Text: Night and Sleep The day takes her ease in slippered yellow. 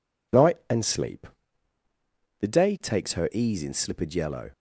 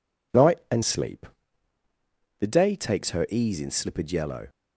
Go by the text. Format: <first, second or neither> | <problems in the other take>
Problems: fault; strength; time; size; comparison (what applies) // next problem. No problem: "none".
neither | pauses between "Sleep" and "The"; the same in both